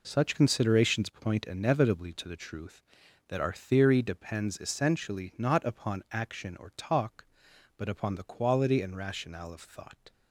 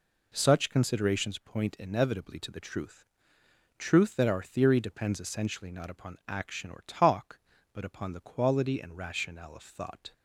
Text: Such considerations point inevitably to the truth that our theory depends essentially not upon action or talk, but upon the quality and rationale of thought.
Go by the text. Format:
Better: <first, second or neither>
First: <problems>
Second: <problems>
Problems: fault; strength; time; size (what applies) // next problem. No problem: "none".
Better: first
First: none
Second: says "truth" twice; at 3.7 s